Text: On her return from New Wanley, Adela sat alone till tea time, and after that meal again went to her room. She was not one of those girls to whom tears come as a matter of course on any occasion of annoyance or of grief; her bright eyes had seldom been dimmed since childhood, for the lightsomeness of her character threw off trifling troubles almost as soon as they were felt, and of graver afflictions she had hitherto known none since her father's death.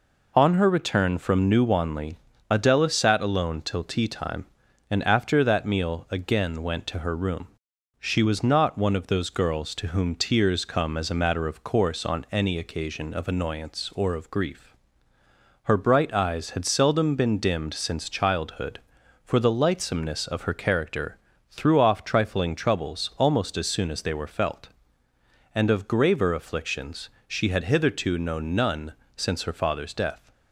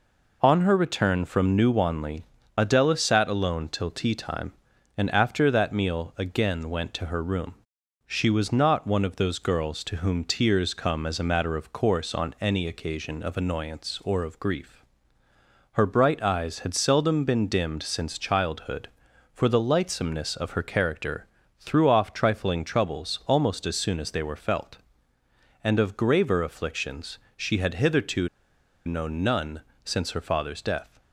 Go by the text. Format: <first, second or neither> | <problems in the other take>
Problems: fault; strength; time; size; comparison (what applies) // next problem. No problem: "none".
first | pauses between "character" and "threw"; slight; at 21.2 s; 0.32 s long; slight in the first // pauses between "afflictions" and "she"; slight; at 27.1 s; 0.18 s long; slight in the first // pauses between "hitherto" and "known"; noticeable; at 28.2 s; 0.58 s long // pauses between "none" and "since"; slight; at 29.6 s; 0.24 s long; slight in the first